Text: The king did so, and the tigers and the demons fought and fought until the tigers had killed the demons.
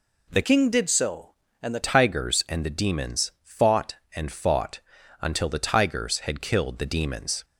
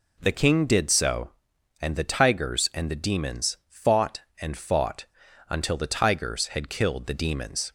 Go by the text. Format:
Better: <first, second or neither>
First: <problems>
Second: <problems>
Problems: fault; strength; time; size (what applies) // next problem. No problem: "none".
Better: second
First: changes voice from "king" to "the"; from 0.4 to 1.8 s; 1.4 s long // pauses between "fought" and "until"; at 4.8 s; 0.40 s long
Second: pauses between "fought" and "until"; at 5.0 s; 0.42 s long